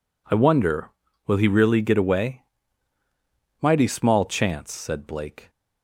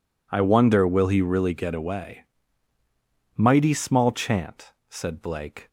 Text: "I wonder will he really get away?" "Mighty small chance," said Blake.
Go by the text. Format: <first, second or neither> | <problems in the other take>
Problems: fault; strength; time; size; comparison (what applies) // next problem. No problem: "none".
first | says "chant" for "chance"; at 4.1 s